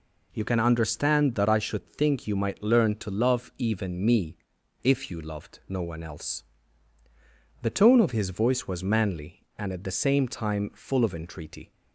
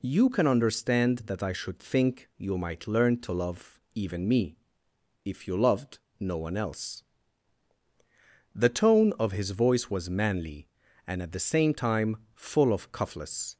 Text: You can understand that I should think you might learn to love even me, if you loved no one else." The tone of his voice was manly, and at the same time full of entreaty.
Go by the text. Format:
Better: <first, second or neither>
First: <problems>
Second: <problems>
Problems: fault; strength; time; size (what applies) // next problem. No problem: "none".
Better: first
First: none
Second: pauses between "loved" and "no"; slight; at 5.9 s; 0.20 s long // pauses between "time" and "full"; slight; at 12.1 s; 0.18 s long // says "cuffless" for "entreaty"; at 12.9 s